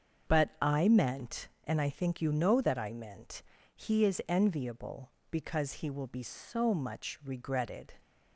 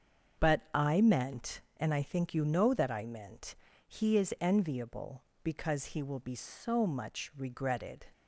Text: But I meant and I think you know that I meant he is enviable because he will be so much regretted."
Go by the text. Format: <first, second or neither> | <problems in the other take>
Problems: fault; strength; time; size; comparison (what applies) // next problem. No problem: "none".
neither | starts louder than the rest; the same in both // pauses between "meant" and "he"; slight; the same in both